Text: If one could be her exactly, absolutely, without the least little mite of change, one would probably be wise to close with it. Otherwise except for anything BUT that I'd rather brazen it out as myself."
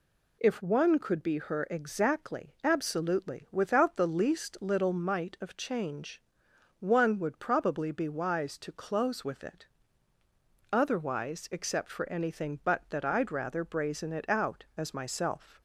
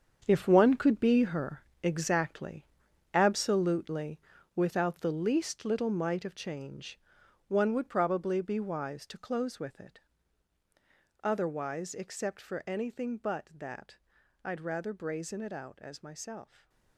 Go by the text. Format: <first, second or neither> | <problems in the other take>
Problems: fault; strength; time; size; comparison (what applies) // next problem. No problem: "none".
first | gets quieter; strong; throughout; 12 dB // pauses between "her" and "exactly"; slight; at 1.6 s; 0.20 s long // pauses between "that" and "I'd"; noticeable; at 13.9 s; 0.48 s long // stays silent after the last word; slight; from 16.4 s on; 0.5 s long